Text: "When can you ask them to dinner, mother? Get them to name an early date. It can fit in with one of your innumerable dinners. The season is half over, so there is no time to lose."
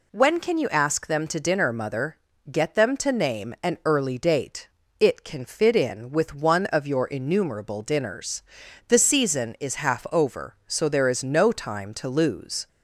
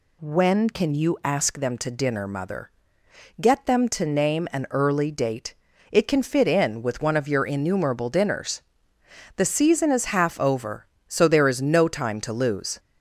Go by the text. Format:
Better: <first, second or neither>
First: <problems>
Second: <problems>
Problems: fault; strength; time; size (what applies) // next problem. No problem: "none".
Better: neither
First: none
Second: none